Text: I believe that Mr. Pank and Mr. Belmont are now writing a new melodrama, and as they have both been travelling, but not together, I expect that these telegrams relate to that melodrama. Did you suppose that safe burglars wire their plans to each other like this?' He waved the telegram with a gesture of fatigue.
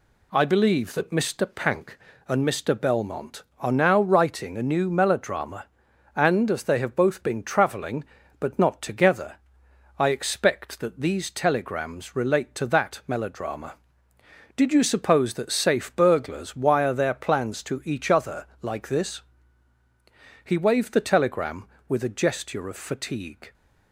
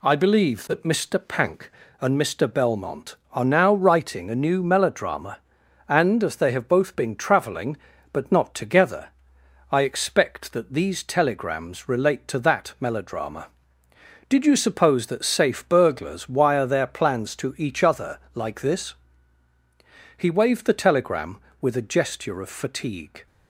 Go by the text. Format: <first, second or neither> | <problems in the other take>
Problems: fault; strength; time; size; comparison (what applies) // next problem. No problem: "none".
neither | none